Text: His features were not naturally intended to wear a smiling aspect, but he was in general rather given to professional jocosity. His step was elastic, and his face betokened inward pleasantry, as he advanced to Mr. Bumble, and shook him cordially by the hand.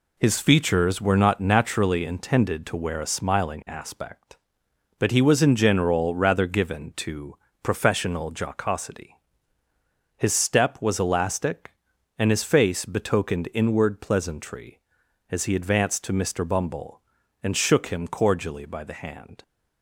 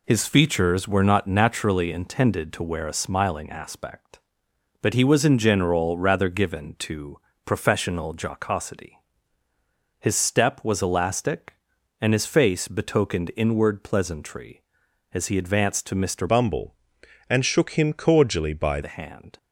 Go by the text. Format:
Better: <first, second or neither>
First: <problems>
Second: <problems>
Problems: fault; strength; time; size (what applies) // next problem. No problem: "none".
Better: first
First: pauses between "to" and "professional"; slight; at 7.3 s; 0.26 s long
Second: pauses between "to" and "professional"; slight; at 7.1 s; 0.26 s long // changes voice from "Bumble" to "by"; from 16.2 to 18.8 s; 2.6 s long